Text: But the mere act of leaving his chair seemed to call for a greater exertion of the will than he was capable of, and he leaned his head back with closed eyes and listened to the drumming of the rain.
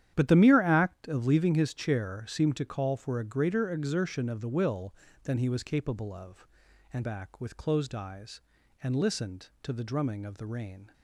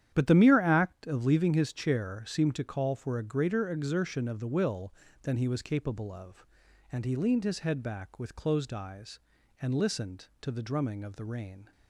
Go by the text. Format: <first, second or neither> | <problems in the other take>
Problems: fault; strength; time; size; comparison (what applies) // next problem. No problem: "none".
second | starts louder than the rest; strong; until 1.1 s; 10.5 dB; strong in the second // skips "he leaned his head"; at 7.0 s